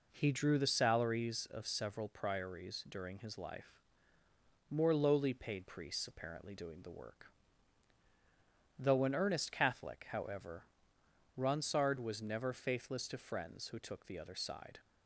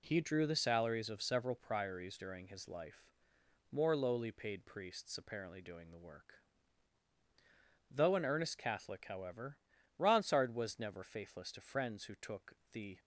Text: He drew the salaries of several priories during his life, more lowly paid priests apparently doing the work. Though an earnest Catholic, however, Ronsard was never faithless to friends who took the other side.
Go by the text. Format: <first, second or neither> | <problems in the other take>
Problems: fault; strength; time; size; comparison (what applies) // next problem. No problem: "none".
first | pauses between "took" and "the"; slight; at 12.5 s; 0.16 s long // stops before "other side"; at 12.9 s